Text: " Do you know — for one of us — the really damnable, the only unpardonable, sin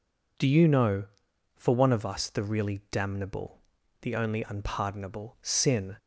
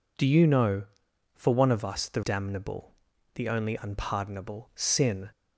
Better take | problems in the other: first | skips "really"; at 2.2 s

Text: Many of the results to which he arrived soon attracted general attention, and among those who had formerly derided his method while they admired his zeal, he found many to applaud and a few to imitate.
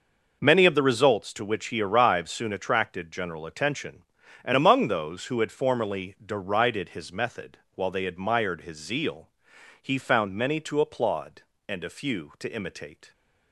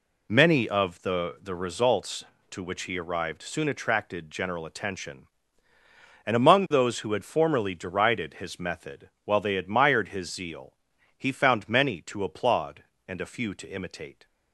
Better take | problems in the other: first | says "the" twice; at 1.4 s // pauses between "method" and "while"; slight; at 9.0 s; 0.16 s long; slight in the first

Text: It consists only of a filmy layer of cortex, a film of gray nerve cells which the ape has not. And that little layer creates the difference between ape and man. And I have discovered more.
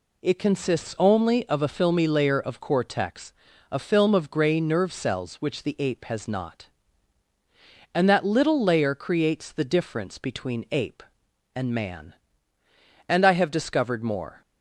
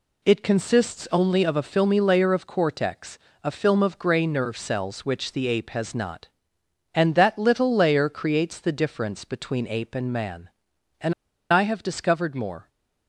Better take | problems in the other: first | pauses between "And" and "I"; at 11.1 s; 0.40 s long

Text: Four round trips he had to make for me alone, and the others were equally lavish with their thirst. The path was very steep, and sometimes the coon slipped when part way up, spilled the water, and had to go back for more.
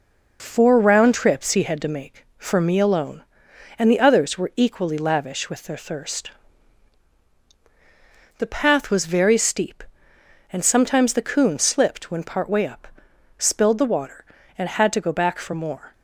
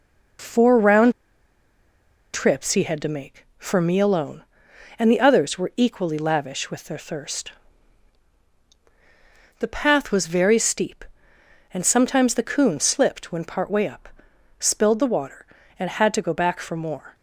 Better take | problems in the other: first | pauses between "round" and "trips"; at 1.1 s; 1.2 s long

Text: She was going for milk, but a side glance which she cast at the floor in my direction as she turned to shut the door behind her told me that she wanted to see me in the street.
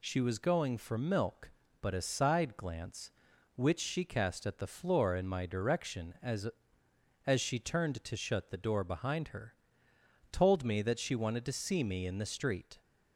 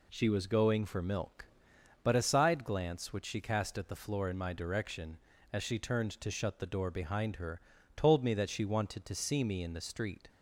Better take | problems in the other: second | says "as" twice; at 7.2 s // pauses between "her" and "told"; noticeable; at 9.5 s; 0.78 s long; slight in the second

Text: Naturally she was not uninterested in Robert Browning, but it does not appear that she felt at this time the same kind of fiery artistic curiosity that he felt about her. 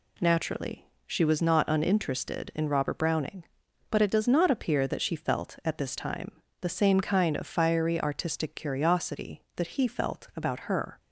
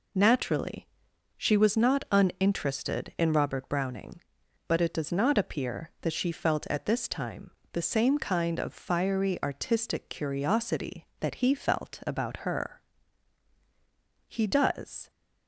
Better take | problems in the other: first | pauses between "Naturally" and "she"; noticeable; at 0.8 s; 0.50 s long; slight in the first // pauses between "time" and "the"; slight; at 7.5 s; 0.20 s long; slight in the first // goes on to say "He does"; noticeable; from 14.2 s on; 0.82 s long

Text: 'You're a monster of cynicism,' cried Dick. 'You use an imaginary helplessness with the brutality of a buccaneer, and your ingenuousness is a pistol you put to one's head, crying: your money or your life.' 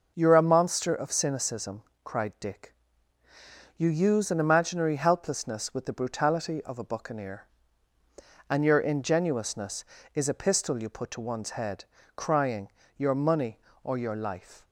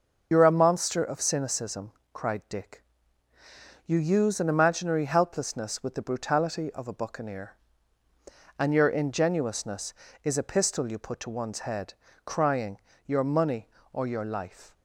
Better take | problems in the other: first | loses the start of "You're"; at 0.3 s; 60 ms

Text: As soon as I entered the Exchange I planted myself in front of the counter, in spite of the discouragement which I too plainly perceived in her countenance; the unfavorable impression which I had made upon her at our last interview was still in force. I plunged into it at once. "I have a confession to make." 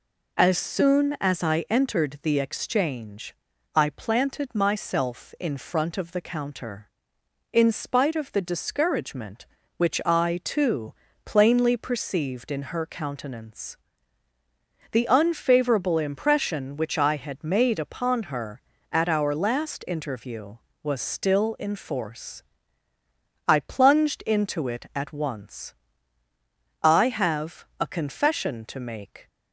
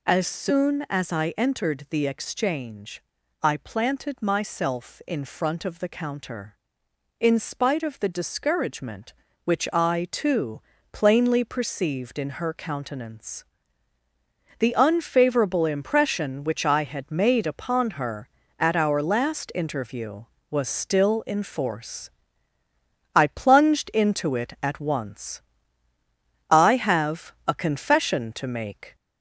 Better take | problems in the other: first | gets louder; slight; throughout; 2.5 dB // pauses between "Exchange" and "I"; at 3.0 s; 0.40 s long; also in the first // pauses between "too" and "plainly"; slight; at 10.6 s; 0.32 s long; slight in the first // pauses between "have" and "a"; slight; at 27.3 s; 0.16 s long; slight in the first

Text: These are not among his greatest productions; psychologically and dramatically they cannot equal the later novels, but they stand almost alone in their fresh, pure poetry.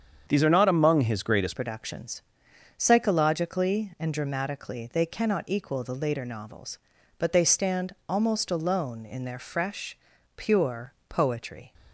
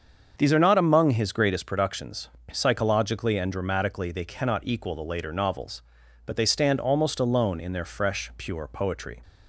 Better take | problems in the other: second | starts louder than the rest; strong; until 1.2 s; 7.5 dB; also in the second // changes voice at "productions"; from 1.5 s on; 10.2 s long // pauses between "pure" and "poetry"; slight; at 10.9 s; 0.16 s long

